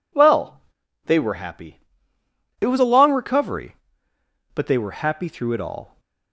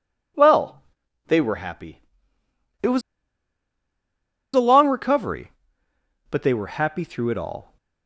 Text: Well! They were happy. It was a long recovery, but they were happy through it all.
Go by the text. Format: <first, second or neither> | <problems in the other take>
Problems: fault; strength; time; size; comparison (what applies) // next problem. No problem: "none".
first | pauses between "was" and "a"; strong; at 3.0 s; 1.5 s long